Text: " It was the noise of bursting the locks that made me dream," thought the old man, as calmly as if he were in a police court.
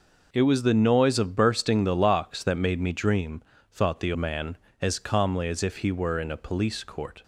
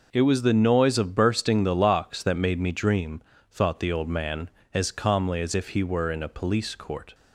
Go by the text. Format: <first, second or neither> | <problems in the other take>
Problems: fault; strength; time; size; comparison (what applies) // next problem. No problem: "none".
second | skips "old"; at 4.1 s